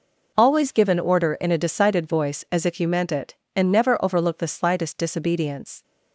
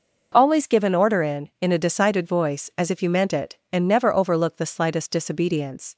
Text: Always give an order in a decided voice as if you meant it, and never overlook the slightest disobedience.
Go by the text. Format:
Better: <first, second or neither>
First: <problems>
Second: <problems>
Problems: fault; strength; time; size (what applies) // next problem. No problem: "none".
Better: first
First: none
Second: says "in" twice; at 1.6 s